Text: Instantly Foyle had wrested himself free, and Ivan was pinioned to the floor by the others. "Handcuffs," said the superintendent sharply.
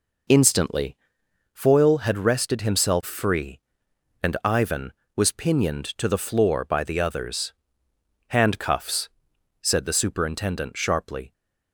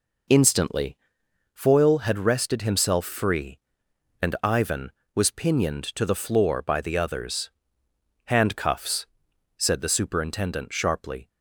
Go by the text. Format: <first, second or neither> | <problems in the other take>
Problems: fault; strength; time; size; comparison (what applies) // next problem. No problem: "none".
neither | pauses between "Instantly" and "Foyle"; noticeable; the same in both